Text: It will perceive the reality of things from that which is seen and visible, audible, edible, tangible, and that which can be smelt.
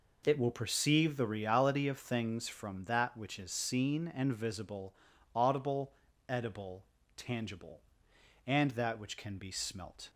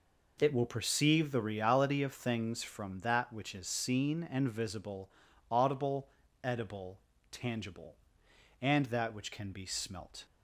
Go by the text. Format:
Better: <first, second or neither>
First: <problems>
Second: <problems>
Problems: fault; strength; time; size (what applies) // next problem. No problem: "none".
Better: neither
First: none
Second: none